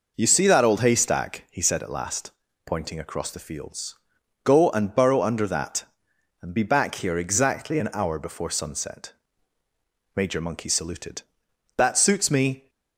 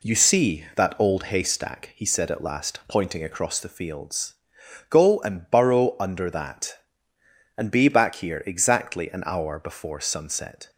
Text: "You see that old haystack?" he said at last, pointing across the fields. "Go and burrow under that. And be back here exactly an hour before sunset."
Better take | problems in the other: second | goes on to say "Major Monkey saluted That suits me"; strong; from 10.1 s on; 2.5 s long

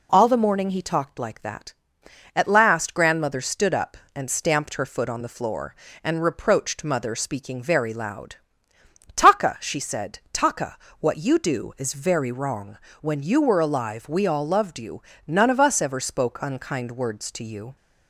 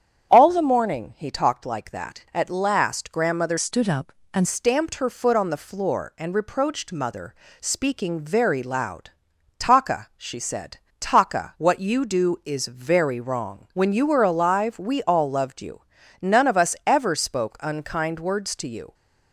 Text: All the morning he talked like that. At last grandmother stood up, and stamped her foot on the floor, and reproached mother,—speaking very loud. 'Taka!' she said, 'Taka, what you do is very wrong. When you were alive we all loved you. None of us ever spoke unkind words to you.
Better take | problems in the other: first | starts louder than the rest; strong; until 1.3 s; 8.5 dB // changes voice from "stood" to "and"; from 3.5 to 4.4 s; 0.9 s long

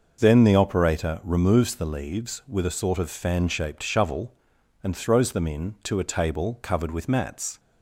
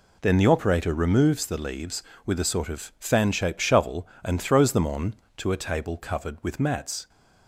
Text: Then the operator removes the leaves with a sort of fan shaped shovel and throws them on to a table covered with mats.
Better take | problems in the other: second | says "in" for "on"; at 5.4 s

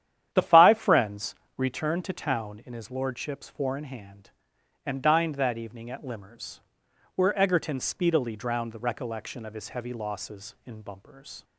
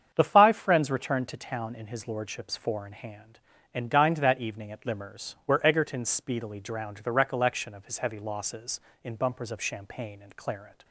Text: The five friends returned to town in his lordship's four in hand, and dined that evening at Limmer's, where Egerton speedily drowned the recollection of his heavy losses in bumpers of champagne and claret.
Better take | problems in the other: second | starts louder than the rest; strong; until 1.3 s; 10.5 dB; strong in the second // pauses between "friends" and "returned"; slight; at 1.3 s; 0.24 s long // stops before "of champagne and claret"; at 11.4 s

